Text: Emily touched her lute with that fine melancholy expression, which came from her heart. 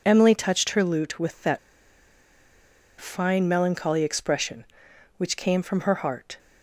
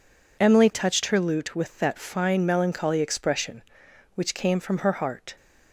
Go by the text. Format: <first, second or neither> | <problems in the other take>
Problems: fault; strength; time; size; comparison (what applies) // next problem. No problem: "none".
second | pauses between "that" and "fine"; strong; at 1.5 s; 1.4 s long